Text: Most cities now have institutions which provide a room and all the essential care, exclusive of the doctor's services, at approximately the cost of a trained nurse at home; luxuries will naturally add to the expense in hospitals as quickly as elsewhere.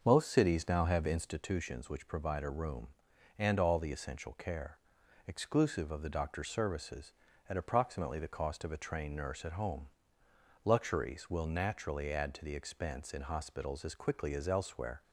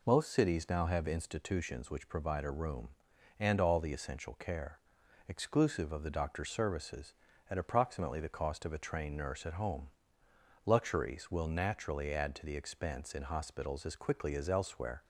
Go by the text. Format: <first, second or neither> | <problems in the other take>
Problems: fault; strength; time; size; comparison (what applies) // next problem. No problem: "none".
second | starts louder than the rest; until 1.5 s; 6.5 dB